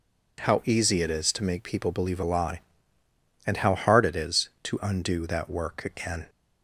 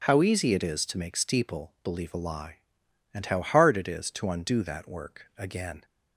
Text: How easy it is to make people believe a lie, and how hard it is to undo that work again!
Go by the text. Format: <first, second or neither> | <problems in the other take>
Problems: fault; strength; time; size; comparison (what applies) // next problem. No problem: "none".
first | says "steeple" for "people"; at 1.1 s